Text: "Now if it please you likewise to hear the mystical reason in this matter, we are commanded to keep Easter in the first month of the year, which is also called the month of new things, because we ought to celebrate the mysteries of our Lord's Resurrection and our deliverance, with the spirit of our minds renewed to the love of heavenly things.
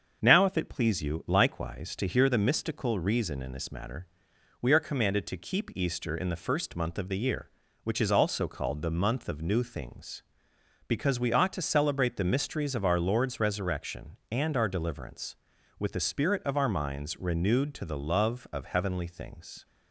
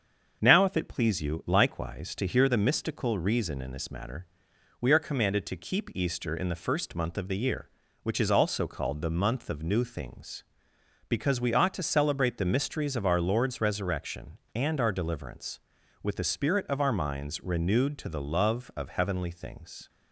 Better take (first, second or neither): neither